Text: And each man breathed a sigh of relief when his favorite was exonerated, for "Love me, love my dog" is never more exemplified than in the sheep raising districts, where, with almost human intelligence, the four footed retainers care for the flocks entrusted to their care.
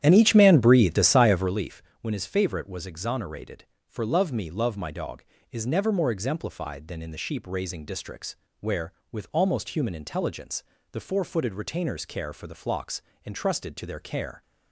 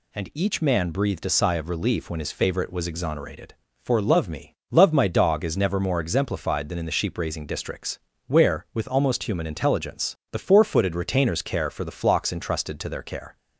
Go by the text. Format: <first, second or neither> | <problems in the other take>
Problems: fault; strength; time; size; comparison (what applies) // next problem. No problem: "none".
second | starts louder than the rest; strong; until 1.7 s; 10.5 dB // pauses between "relief" and "when"; slight; at 1.8 s; 0.18 s long // pauses between "flocks" and "entrusted"; slight; at 13.0 s; 0.24 s long